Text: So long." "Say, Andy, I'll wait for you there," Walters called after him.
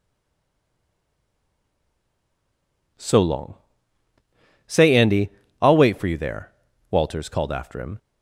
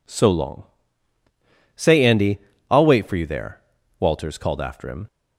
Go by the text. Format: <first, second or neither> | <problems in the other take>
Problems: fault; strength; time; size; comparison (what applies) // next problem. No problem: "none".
second | stays silent before the first word; strong; until 2.9 s; 2.9 s long